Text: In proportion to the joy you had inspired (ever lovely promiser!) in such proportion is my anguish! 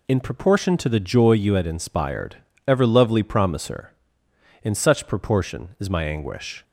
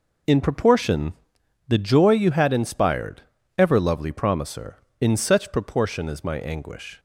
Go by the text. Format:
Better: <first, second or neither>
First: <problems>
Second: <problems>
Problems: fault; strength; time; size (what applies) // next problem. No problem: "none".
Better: first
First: none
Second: skips "to"; at 1.4 s